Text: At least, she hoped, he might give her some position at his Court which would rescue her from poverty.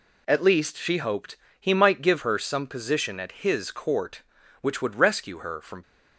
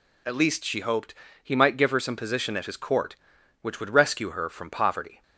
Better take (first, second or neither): second